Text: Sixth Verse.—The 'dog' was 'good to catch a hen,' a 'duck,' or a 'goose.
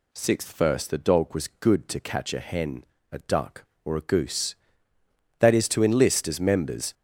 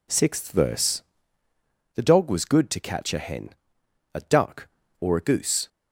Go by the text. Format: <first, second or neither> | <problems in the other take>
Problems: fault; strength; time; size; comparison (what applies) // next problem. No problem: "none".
second | goes on to say "That is to enlist as members"; from 5.3 s on; 1.5 s long